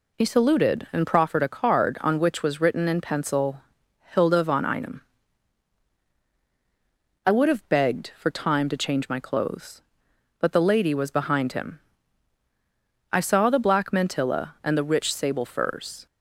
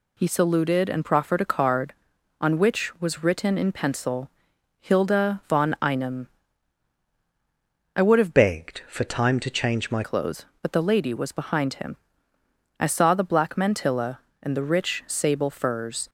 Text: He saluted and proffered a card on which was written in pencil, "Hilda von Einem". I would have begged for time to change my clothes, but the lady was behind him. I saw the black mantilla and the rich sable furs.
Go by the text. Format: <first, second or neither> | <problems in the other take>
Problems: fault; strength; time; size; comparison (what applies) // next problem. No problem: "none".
first | changes voice from "begged" to "my"; from 8.3 to 10.0 s; 1.7 s long